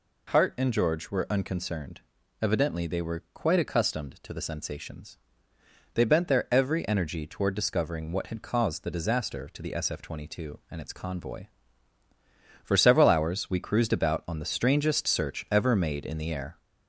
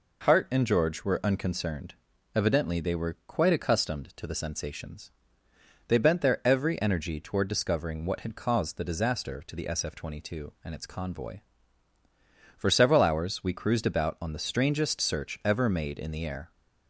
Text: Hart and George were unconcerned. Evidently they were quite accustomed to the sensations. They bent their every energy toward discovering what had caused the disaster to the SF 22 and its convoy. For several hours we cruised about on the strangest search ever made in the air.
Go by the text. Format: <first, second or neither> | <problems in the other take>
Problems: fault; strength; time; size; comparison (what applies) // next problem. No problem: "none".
second | gets louder; slight; throughout; 2.5 dB